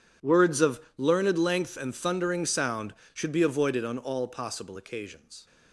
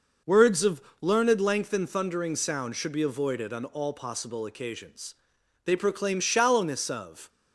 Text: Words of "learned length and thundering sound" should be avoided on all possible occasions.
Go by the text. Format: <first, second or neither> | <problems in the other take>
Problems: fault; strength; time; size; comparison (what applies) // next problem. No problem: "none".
first | pauses between "of" and "learned"; slight; at 0.8 s; 0.20 s long; slight in the first // goes on to say "They proclaim shallowness of"; from 5.6 s on; 1.6 s long